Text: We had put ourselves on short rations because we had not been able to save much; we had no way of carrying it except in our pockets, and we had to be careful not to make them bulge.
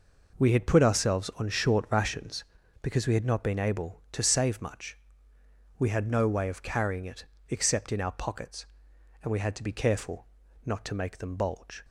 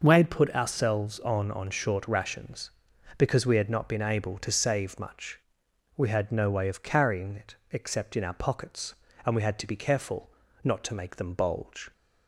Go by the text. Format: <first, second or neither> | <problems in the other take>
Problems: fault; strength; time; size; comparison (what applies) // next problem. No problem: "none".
first | says "on" twice; at 1.5 s // pauses between "it" and "except"; slight; at 7.5 s; 0.16 s long; slight in the first // pauses between "careful" and "not"; slight; at 10.2 s; 0.36 s long; also in the first